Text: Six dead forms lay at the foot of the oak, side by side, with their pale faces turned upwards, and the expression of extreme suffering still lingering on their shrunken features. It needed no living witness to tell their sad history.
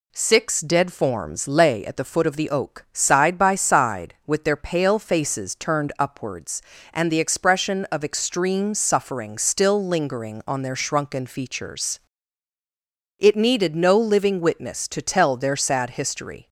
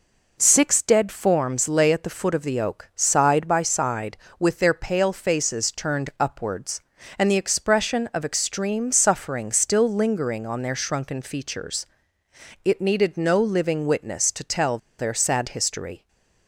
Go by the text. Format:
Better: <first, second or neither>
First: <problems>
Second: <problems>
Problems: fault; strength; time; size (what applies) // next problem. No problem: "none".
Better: first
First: none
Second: pauses between "tell" and "their"; slight; at 14.7 s; 0.21 s long // stays silent after the last word; slight; from 15.9 s on; 0.5 s long